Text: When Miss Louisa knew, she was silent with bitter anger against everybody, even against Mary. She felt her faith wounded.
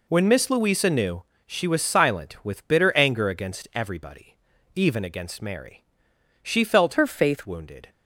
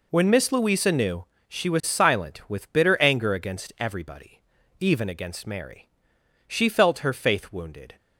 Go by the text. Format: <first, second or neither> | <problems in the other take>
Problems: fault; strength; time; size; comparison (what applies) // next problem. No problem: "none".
second | changes voice from "her" to "faith"; from 6.9 to 7.4 s; 0.5 s long